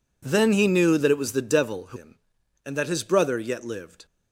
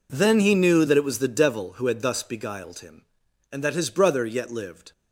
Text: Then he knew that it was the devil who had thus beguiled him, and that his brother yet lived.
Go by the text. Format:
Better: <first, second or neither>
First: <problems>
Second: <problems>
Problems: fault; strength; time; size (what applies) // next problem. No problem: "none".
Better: second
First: skips "had thus beguiled"; at 1.9 s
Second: none